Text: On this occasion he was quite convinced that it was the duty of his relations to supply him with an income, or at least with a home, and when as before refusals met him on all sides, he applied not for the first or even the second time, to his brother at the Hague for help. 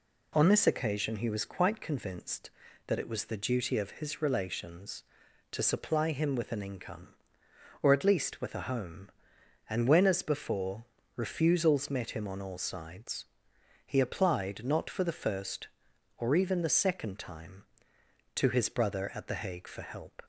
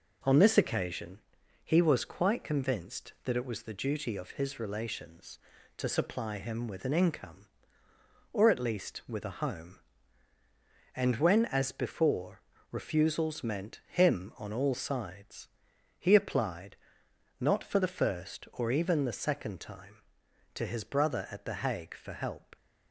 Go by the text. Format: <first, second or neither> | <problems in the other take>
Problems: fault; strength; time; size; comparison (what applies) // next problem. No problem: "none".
first | pauses between "occasion" and "he"; at 1.1 s; 0.44 s long // pauses between "before" and "refusals"; slight; at 12.4 s; 0.28 s long; slight in the first // says "meant" for "met"; at 13.4 s // pauses between "applied" and "not"; noticeable; at 16.7 s; 0.64 s long